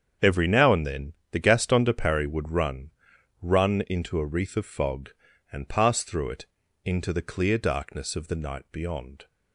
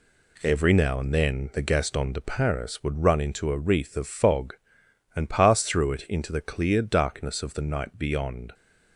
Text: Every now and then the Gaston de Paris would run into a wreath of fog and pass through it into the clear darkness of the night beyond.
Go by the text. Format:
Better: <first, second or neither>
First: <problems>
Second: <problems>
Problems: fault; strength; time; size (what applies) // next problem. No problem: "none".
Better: second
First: starts louder than the rest; strong; until 1.3 s; 7.5 dB // pauses between "then" and "the"; slight; at 1.1 s; 0.18 s long // says "run" twice; at 3.4 s // pauses between "it" and "into"; at 6.4 s; 0.38 s long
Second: none